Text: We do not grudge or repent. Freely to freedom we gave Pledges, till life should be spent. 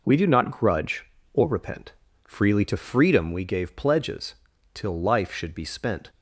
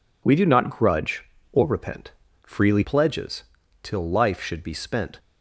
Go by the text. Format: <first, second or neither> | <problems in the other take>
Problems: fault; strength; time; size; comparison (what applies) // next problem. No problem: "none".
first | skips "to freedom we gave"; at 2.8 s